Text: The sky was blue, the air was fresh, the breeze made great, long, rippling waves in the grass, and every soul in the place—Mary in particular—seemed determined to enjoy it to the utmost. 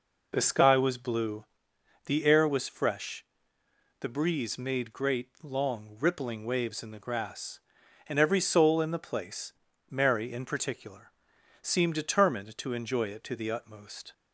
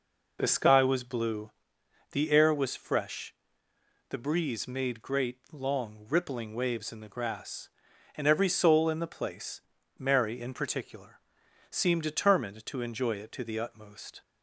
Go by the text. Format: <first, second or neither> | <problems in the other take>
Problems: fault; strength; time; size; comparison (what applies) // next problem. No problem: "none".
neither | none